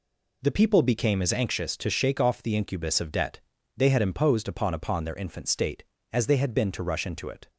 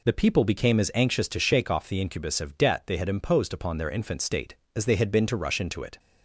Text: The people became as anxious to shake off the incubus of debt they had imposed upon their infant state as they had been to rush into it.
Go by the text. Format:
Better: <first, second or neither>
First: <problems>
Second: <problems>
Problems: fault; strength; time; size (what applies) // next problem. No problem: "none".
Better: second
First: pauses between "debt" and "they"; slight; at 3.3 s; 0.36 s long // says "upon" twice; at 4.7 s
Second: none